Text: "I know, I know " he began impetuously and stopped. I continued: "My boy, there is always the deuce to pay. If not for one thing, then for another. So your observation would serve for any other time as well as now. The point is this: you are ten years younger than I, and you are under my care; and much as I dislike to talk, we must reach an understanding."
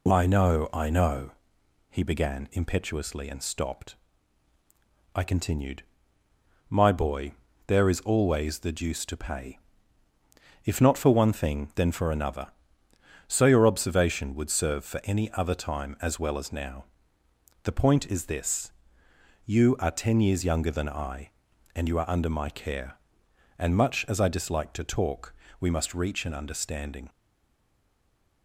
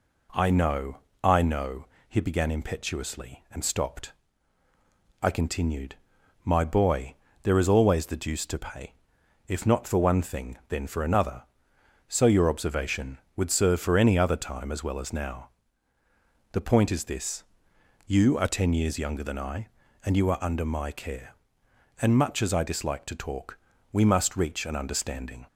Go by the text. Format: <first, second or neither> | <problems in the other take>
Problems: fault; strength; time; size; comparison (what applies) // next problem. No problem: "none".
second | stays silent after the last word; noticeable; from 27.0 s on; 1.4 s long